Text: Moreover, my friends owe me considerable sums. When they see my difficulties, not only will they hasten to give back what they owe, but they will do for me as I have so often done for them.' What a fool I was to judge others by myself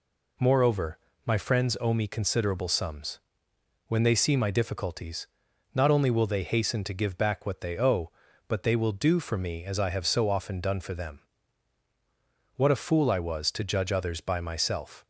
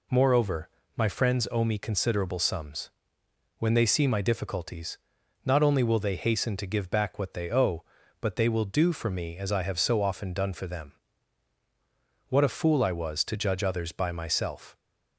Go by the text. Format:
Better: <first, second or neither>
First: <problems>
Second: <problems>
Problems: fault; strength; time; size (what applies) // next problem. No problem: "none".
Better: neither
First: none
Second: none